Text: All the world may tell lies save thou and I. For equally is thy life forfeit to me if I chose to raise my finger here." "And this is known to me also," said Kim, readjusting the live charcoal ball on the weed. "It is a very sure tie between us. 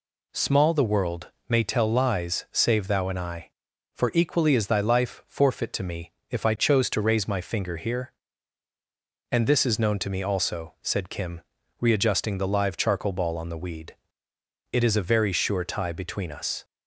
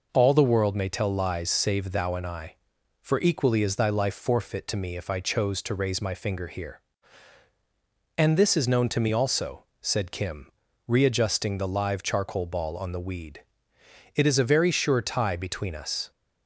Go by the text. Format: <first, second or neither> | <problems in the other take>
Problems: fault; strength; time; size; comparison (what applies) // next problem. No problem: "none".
second | says "Small" for "All"; at 0.3 s // pauses between "world" and "may"; slight; at 1.3 s; 0.16 s long // pauses between "me" and "if"; slight; at 6.1 s; 0.18 s long